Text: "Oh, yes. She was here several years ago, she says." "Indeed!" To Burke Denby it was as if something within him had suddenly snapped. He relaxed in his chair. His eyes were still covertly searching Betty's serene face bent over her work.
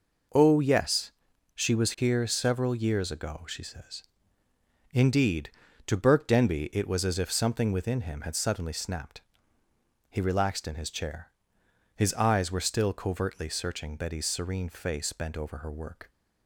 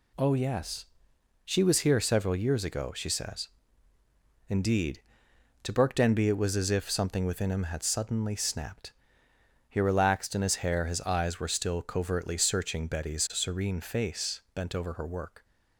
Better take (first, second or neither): first